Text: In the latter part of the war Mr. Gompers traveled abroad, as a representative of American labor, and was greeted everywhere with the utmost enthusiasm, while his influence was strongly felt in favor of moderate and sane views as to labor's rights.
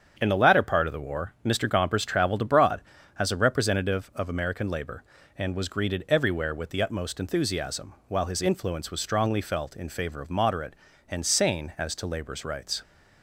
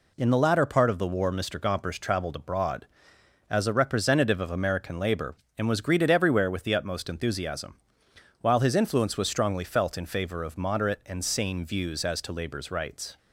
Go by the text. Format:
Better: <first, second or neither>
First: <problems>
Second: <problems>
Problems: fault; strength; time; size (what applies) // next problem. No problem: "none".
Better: second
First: starts louder than the rest; strong; until 1.2 s; 7.5 dB // skips "views"; at 11.7 s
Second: none